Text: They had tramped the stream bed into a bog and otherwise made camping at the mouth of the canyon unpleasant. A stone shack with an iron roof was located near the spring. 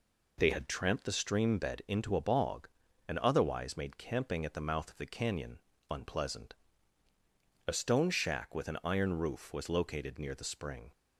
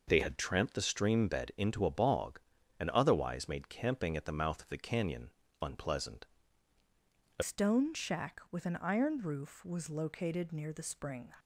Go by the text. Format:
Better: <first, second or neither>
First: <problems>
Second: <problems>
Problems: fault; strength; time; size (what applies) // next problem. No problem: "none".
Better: first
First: pauses between "canyon" and "unpleasant"; slight; at 5.5 s; 0.30 s long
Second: pauses between "canyon" and "unpleasant"; slight; at 5.3 s; 0.30 s long // changes voice at "stone"; from 7.4 s on; 3.9 s long